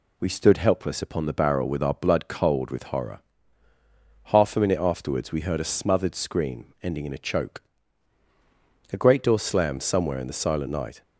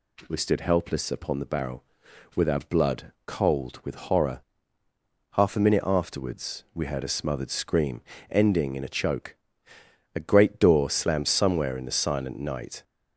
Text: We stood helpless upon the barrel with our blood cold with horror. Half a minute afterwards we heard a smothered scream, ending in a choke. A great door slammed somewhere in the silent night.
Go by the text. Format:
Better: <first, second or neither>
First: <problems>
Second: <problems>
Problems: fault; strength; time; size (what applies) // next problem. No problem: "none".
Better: neither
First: none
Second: none